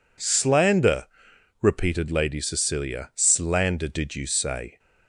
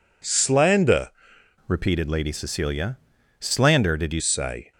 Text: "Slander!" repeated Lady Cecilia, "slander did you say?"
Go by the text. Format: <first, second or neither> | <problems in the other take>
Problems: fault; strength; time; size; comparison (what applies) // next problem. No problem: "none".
first | changes voice from "repeated" to "you"; from 1.6 to 4.2 s; 2.6 s long